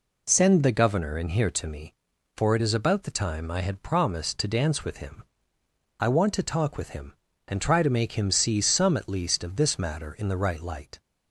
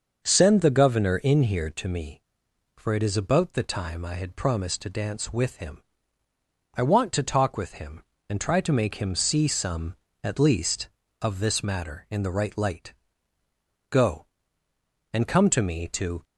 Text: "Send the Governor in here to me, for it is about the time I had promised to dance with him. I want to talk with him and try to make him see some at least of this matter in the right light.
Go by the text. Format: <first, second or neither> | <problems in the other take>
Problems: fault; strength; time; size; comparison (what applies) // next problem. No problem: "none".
first | starts louder than the rest; until 1.2 s; 6.5 dB // goes on to say "Go and come to me to"; strong; from 13.8 s on; 2.3 s long